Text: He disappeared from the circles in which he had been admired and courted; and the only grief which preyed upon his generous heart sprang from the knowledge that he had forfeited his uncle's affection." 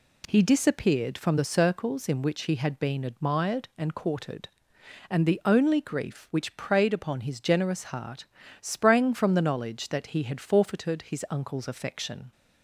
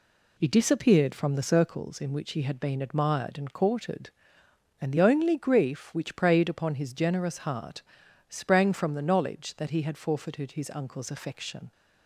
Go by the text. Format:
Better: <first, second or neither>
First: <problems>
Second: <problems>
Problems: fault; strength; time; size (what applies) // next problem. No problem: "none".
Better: neither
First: pauses between "heart" and "sprang"; slight; at 8.2 s; 0.36 s long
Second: pauses between "heart" and "sprang"; noticeable; at 7.8 s; 0.46 s long